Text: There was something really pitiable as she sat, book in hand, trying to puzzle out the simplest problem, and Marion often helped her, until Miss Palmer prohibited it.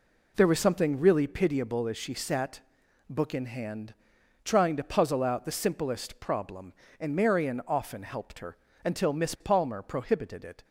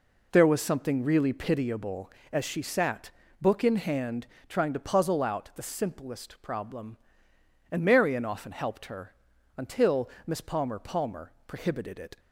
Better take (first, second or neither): first